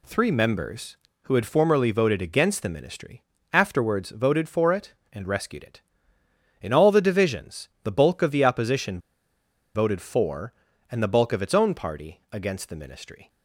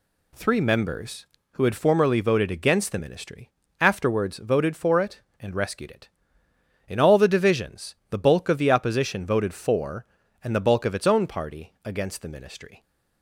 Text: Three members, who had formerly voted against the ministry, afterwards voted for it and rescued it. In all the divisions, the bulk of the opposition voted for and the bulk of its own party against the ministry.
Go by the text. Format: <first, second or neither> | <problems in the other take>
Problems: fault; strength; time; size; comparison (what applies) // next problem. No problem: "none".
second | pauses between "opposition" and "voted"; noticeable; at 8.9 s; 0.76 s long